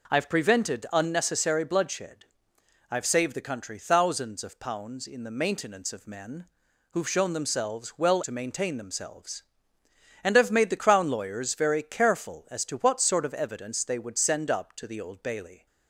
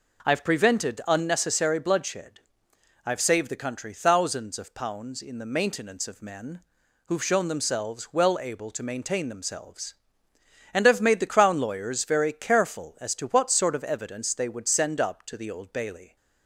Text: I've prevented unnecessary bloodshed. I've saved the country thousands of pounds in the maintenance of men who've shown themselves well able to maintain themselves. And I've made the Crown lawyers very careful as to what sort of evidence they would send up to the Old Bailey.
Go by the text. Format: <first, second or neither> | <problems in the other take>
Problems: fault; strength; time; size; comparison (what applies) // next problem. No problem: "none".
second | pauses between "men" and "who've"; noticeable; at 6.4 s; 0.46 s long; noticeable in the second // skips "able"; at 8.2 s